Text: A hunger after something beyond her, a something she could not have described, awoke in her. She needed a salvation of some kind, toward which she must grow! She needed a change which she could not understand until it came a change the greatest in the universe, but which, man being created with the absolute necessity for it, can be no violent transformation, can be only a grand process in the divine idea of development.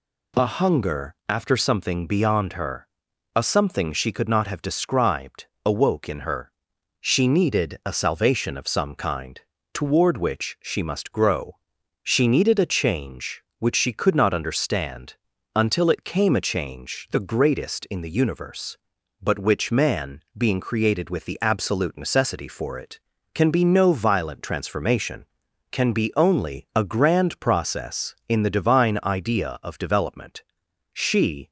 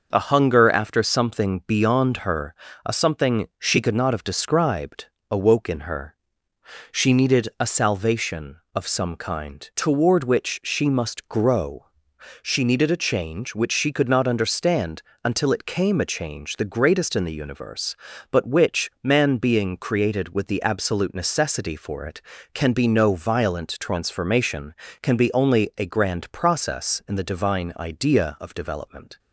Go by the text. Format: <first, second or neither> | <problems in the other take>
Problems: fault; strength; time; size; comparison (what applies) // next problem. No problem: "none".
second | pauses between "understand" and "until"; at 15.1 s; 0.42 s long; slight in the second // goes on to say "She"; from 30.9 s on; 0.58 s long